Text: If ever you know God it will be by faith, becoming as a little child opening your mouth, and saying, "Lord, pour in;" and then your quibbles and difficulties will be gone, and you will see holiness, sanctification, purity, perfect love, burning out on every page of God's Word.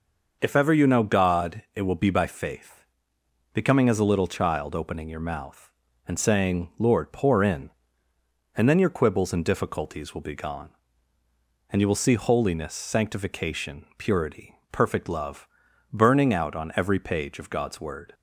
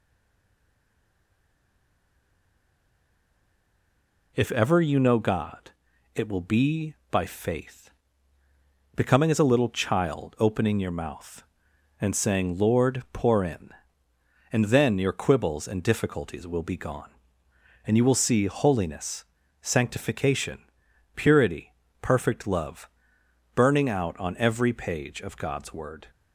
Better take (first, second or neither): first